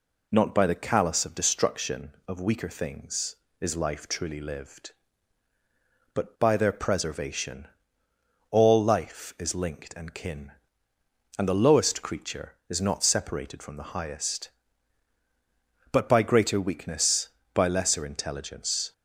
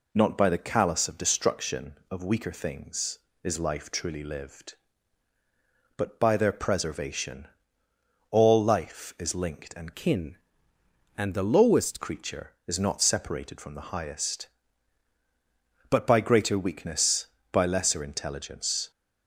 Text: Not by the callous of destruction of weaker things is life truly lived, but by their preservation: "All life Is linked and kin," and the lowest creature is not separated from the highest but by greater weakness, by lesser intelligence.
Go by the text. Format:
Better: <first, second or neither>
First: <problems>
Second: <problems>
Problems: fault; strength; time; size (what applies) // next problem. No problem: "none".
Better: first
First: none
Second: changes voice from "kin" to "lowest"; from 9.9 to 12.0 s; 2.1 s long